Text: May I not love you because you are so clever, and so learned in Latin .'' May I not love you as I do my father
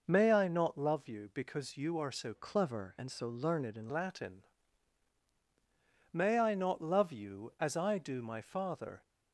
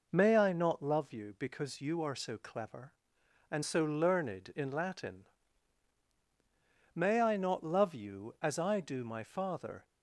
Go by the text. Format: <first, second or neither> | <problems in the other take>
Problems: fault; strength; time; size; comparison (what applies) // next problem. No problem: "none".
second | starts louder than the rest; until 1.0 s; 6 dB // changes voice from "clever" to "in"; from 2.3 to 3.9 s; 1.6 s long